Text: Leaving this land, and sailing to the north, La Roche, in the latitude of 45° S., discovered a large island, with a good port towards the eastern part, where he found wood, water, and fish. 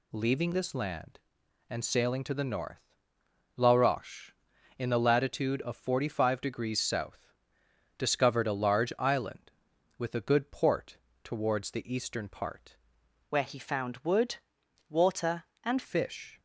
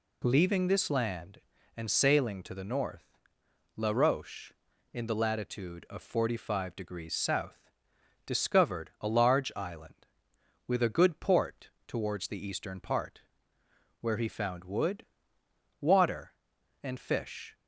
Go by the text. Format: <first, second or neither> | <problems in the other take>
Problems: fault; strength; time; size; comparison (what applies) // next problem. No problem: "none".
second | pauses between "port" and "towards"; slight; at 10.9 s; 0.26 s long; slight in the second // changes voice from "where" to "and"; from 13.3 to 15.8 s; 2.5 s long